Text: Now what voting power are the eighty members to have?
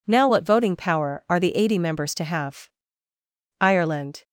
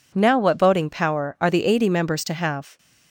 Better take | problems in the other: second | goes on to say "Ireland"; noticeable; from 3.5 s on; 0.64 s long

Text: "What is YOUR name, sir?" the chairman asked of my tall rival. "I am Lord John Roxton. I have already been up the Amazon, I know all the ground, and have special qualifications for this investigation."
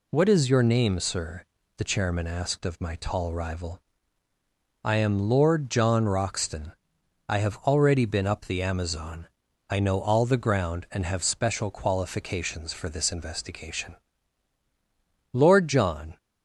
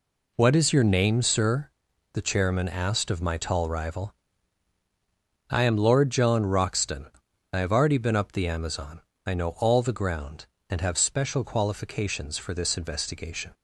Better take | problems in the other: second | goes on to say "Lord John"; noticeable; from 15.3 s on; 0.86 s long

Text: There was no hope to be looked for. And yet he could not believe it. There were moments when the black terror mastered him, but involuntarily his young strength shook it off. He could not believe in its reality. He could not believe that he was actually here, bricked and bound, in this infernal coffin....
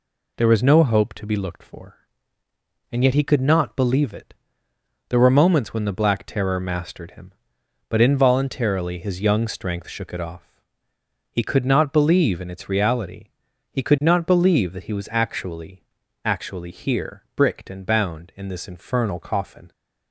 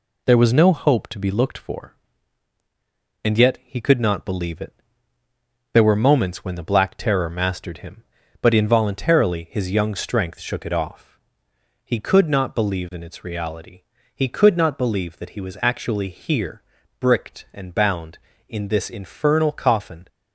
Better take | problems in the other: second | says "actually" twice; at 16.2 s

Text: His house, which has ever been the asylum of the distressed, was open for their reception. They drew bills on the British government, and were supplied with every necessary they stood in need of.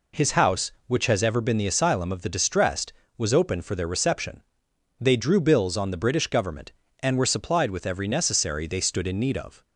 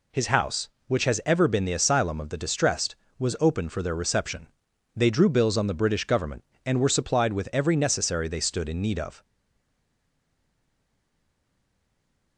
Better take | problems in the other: first | stays silent after the last word; strong; from 9.2 s on; 3.1 s long

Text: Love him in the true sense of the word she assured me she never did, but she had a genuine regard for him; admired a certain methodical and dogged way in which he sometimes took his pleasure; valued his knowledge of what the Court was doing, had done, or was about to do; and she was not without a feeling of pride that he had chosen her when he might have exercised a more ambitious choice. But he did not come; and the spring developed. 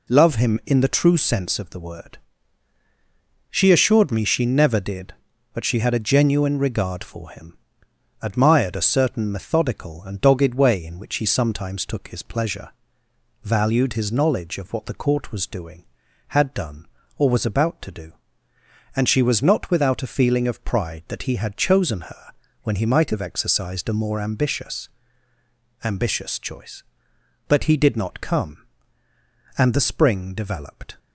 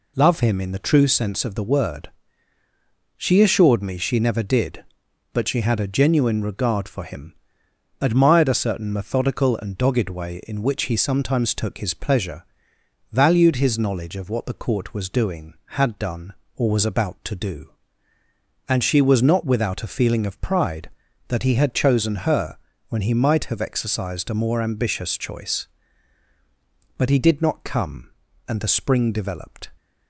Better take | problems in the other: second | pauses between "word" and "she"; strong; at 2.1 s; 1.3 s long; also in the second // pauses between "her" and "when"; slight; at 22.3 s; 0.30 s long; slight in the second // says "ambitious" twice; at 25.8 s

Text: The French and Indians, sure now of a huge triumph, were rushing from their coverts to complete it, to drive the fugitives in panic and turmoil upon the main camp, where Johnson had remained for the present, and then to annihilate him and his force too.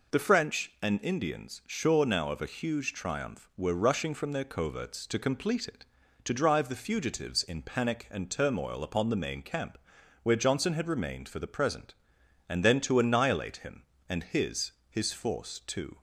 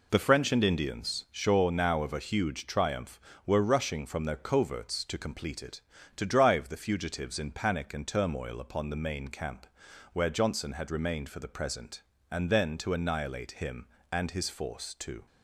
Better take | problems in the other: second | says "his" twice; at 14.8 s

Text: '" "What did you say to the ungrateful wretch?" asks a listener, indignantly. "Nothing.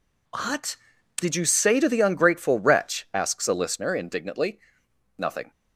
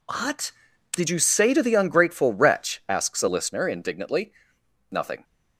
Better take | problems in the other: neither | none

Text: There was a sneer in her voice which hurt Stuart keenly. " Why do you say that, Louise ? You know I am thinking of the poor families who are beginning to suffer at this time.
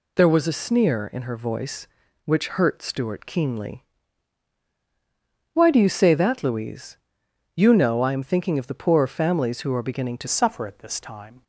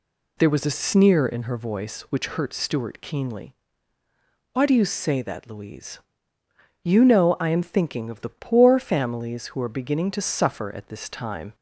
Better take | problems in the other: second | changes voice at "suffer"; from 10.2 s on; 1.2 s long

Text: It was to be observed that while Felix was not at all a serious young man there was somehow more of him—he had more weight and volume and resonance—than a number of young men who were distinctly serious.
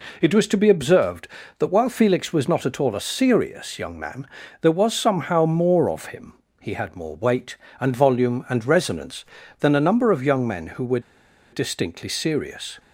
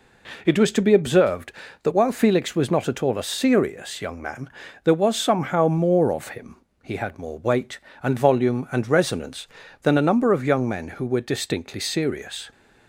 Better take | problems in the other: second | pauses between "man" and "there"; slight; at 4.2 s; 0.36 s long; slight in the second // pauses between "were" and "distinctly"; noticeable; at 10.9 s; 0.52 s long

